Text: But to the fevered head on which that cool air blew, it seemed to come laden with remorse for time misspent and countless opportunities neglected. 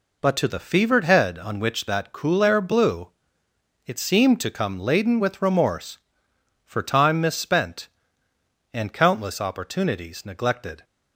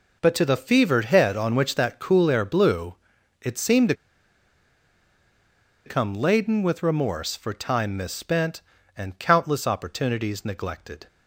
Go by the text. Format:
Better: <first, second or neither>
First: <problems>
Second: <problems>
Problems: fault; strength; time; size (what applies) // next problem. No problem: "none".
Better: first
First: none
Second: pauses between "to" and "come"; strong; at 3.9 s; 1.9 s long